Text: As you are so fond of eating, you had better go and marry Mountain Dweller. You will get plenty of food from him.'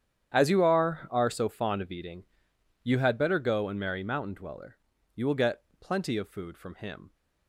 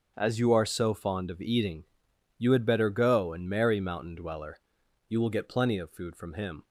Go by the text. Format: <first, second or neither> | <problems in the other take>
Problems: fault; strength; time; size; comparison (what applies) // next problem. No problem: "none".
second | starts louder than the rest; strong; until 1.3 s; 9.5 dB; also in the second // says "are" twice; at 1.1 s // pauses between "get" and "plenty"; slight; at 5.6 s; 0.18 s long